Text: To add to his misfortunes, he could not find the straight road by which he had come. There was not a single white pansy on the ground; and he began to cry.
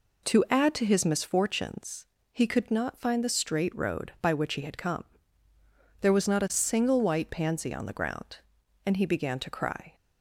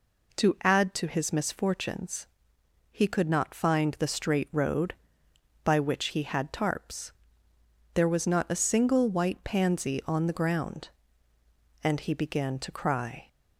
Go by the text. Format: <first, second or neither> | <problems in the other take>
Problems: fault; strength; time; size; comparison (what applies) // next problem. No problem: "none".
first | says "tarps" for "come"; at 6.5 s